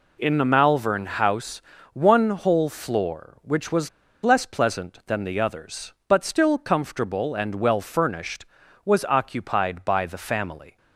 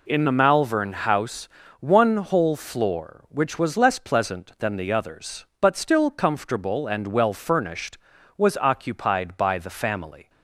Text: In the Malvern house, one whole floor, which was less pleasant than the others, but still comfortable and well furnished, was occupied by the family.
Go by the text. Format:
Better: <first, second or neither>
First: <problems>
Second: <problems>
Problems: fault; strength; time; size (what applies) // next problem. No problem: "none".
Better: second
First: pauses between "was" and "less"; slight; at 3.8 s; 0.33 s long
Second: none